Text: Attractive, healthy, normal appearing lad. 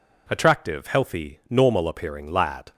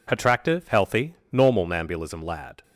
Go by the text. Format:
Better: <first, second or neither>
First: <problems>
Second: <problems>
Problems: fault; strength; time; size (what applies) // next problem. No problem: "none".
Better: first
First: none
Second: says "nambulism" for "appearing"; at 1.6 s